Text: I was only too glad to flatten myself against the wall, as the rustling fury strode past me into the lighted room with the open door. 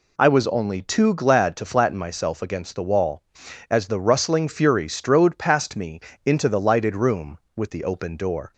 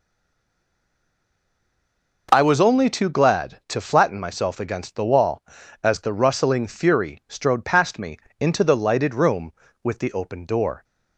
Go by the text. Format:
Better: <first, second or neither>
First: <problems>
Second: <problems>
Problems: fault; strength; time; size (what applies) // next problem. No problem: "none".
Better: first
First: pauses between "me" and "into"; slight; at 5.9 s; 0.26 s long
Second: stays silent before the first word; until 2.2 s; 2.2 s long // pauses between "me" and "into"; slight; at 8.1 s; 0.20 s long